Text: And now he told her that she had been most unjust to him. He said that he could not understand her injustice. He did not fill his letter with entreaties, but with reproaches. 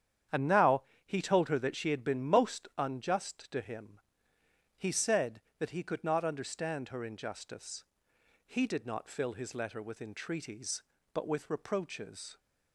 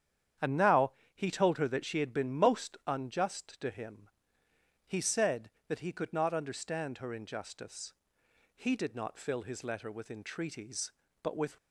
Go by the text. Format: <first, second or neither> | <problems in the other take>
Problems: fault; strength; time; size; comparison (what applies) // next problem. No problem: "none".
first | starts louder than the rest; strong; until 1.6 s; 9 dB; strong in the first // pauses between "now" and "he"; slight; at 0.9 s; 0.24 s long; slight in the first // stops before "reproaches"; at 11.5 s